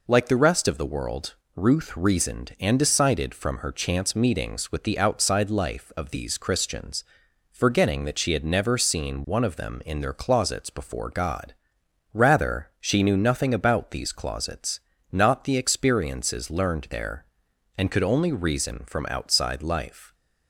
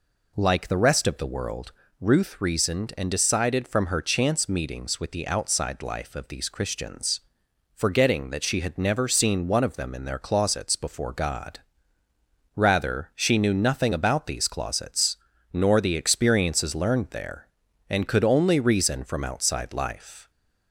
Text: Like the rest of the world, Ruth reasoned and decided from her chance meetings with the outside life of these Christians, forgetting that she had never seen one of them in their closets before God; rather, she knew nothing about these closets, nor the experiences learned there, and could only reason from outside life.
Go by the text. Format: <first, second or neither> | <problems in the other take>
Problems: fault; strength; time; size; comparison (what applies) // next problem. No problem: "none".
second | says "not" for "nor"; at 15.1 s